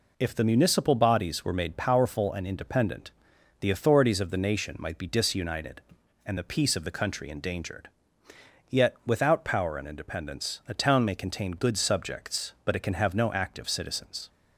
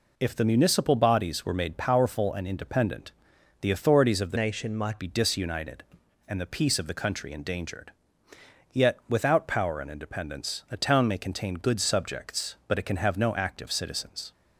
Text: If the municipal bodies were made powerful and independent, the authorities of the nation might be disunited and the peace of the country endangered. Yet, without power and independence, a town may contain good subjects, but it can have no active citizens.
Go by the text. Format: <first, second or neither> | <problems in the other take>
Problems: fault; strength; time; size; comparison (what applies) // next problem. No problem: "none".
first | changes voice from "nation" to "might"; from 4.3 to 4.9 s; 0.6 s long